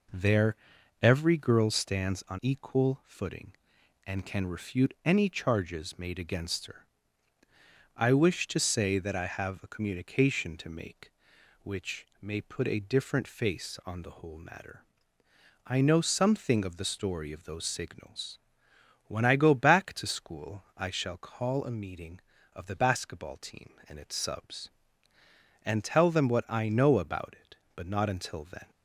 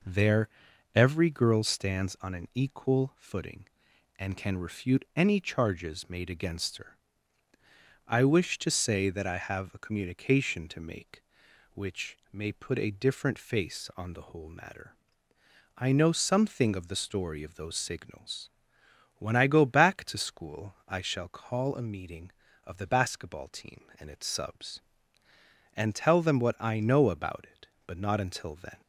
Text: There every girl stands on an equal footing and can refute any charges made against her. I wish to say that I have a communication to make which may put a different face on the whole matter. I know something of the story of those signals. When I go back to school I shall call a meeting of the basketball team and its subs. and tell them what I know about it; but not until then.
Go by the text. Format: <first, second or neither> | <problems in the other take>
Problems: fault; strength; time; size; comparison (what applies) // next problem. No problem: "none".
second | pauses between "There" and "every"; noticeable; at 0.5 s; 0.46 s long; noticeable in the second // skips "an"; at 2.4 s // pauses between "which" and "may"; slight; at 12.0 s; 0.16 s long; slight in the second // pauses between "school" and "I"; slight; at 20.6 s; 0.16 s long; slight in the second